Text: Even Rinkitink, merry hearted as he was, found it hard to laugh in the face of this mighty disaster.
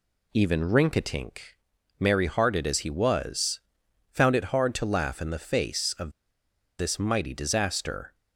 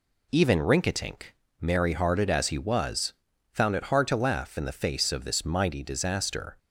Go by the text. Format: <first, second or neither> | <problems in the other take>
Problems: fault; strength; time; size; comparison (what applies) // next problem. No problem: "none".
second | pauses between "of" and "this"; noticeable; at 6.1 s; 0.67 s long